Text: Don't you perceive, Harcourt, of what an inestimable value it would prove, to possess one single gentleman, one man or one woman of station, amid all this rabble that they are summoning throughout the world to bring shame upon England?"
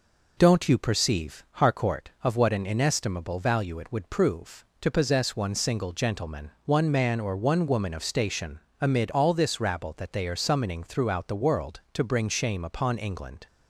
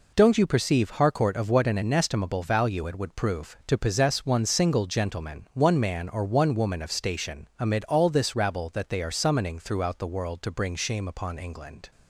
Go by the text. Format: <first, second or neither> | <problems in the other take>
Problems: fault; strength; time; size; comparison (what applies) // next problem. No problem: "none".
neither | none